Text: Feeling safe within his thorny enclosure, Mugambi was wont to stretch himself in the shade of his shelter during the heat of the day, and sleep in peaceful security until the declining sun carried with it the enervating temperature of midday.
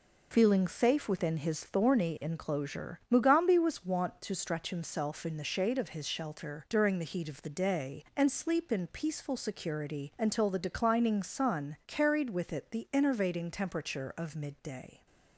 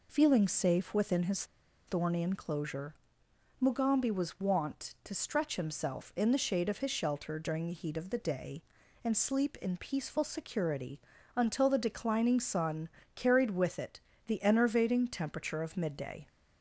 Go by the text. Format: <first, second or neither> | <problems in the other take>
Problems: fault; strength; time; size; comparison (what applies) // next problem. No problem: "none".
first | pauses between "his" and "thorny"; at 1.4 s; 0.42 s long // pauses between "security" and "until"; at 10.9 s; 0.38 s long // pauses between "sun" and "carried"; slight; at 12.8 s; 0.26 s long // pauses between "it" and "the"; slight; at 14.0 s; 0.26 s long